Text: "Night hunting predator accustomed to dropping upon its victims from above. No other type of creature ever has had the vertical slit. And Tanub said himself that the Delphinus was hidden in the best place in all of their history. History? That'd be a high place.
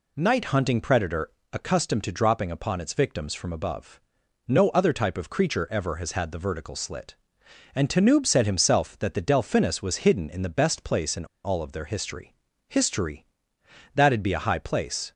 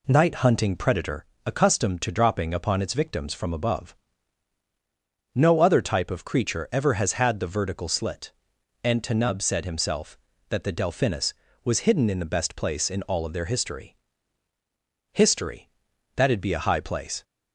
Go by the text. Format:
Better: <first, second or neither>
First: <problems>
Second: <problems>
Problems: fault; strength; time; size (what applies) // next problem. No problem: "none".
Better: second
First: pauses between "predator" and "accustomed"; slight; at 1.3 s; 0.20 s long // pauses between "in" and "all"; slight; at 11.2 s; 0.18 s long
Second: pauses between "predator" and "accustomed"; slight; at 1.2 s; 0.22 s long